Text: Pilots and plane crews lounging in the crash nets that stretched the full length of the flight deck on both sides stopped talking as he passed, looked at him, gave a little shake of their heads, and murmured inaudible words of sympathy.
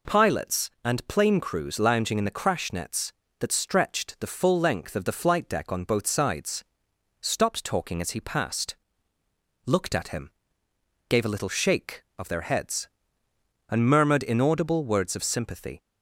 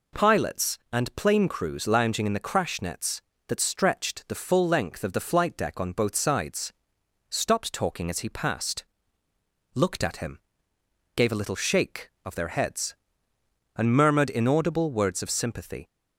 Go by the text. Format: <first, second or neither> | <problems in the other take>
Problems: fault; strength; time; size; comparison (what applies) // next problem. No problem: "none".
neither | pauses between "sides" and "stopped"; noticeable; the same in both